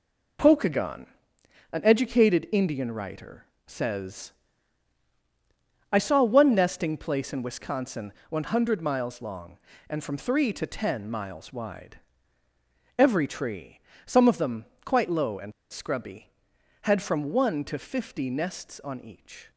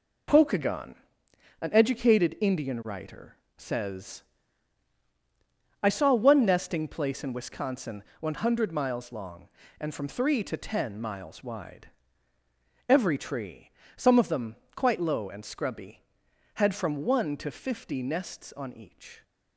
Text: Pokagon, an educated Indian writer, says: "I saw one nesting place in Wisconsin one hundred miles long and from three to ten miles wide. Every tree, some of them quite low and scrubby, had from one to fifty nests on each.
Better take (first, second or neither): second